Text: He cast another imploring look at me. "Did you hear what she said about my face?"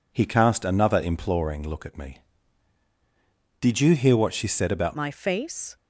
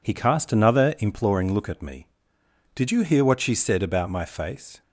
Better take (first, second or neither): second